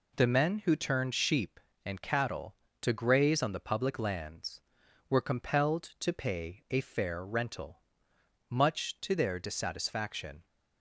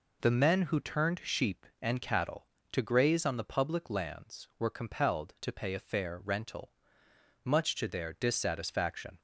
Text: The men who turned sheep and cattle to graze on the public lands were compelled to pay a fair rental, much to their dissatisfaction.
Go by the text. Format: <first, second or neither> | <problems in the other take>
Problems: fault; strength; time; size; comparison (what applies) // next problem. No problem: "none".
neither | none